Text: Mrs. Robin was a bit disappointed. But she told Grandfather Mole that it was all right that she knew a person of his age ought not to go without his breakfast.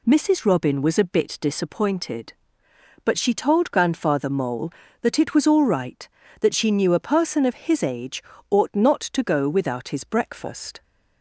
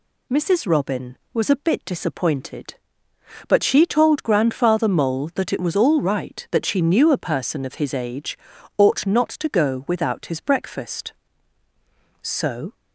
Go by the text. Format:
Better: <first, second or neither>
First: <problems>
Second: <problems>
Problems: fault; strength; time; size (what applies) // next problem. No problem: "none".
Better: first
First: pauses between "age" and "ought"; slight; at 8.2 s; 0.28 s long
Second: pauses between "age" and "ought"; at 8.3 s; 0.40 s long // goes on to say "So"; from 12.2 s on; 0.52 s long